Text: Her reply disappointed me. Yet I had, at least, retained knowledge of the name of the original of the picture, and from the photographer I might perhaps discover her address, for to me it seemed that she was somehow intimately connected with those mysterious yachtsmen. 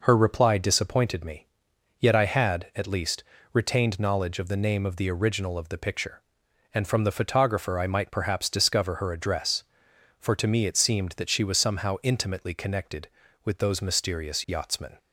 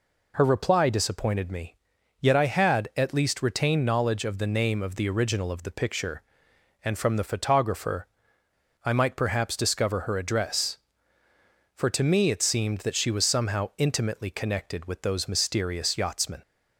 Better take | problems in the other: first | pauses between "photographer" and "I"; noticeable; at 8.0 s; 0.76 s long

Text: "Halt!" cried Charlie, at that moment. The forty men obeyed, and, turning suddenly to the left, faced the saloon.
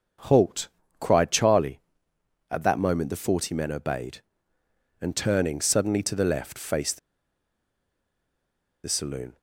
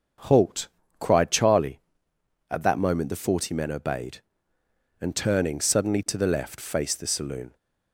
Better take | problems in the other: second | starts louder than the rest; until 1.5 s; 6.5 dB; also in the second // pauses between "faced" and "the"; strong; at 6.9 s; 1.8 s long

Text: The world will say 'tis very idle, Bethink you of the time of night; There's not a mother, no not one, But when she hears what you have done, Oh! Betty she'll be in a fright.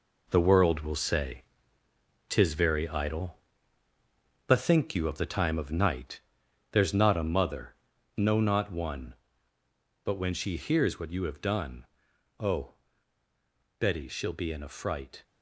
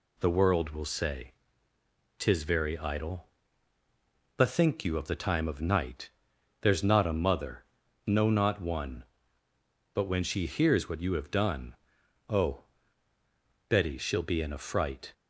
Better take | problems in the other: second | gets quieter; strong; throughout; 7.5 dB // pauses between "say" and "tis"; noticeable; at 1.4 s; 0.84 s long; noticeable in the second

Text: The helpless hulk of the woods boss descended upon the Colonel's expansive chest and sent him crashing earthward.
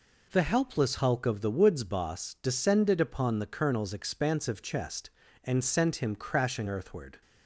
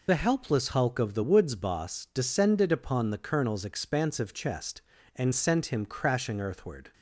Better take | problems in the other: first | loses the start of "The"; at 0.0 s; 50 ms

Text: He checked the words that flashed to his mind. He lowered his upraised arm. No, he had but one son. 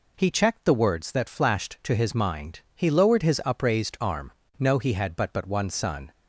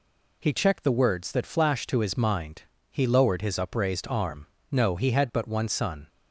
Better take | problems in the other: second | says "but" twice; at 5.3 s

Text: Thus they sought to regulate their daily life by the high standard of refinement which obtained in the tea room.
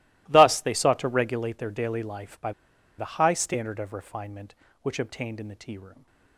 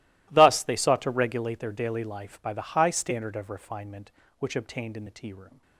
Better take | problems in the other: second | starts louder than the rest; strong; until 1.2 s; 17.5 dB; strong in the second // pauses between "by" and "the"; noticeable; at 2.5 s; 0.46 s long

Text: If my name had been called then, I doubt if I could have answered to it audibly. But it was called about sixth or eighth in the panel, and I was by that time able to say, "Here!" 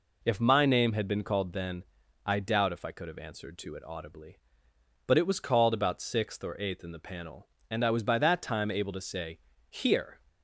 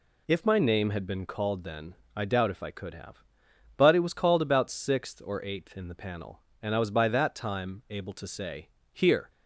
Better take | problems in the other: first | skips "answered to it audibly"; at 3.5 s

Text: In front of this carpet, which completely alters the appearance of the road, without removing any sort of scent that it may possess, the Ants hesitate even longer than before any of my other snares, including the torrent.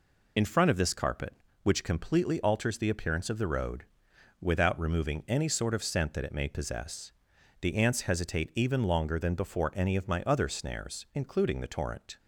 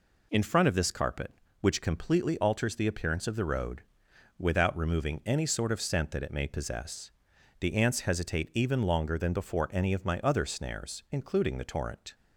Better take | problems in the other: second | loses the start of "In"; at 0.3 s; 30 ms

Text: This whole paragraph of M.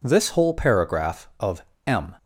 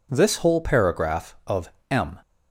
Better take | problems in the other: neither | pauses between "of" and "M"; slight; the same in both

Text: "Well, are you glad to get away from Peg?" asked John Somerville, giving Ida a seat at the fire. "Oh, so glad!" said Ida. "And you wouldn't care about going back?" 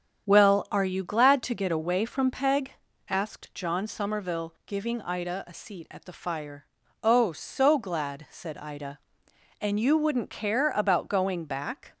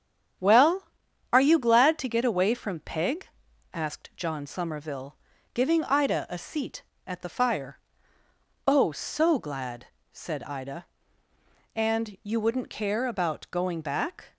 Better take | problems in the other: neither | starts louder than the rest; strong; the same in both

